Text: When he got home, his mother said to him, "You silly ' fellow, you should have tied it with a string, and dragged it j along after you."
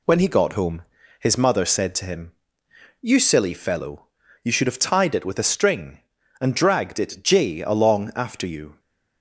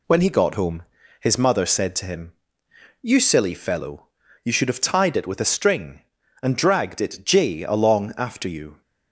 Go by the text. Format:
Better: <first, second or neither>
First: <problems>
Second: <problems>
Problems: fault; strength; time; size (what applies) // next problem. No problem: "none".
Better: neither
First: none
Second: none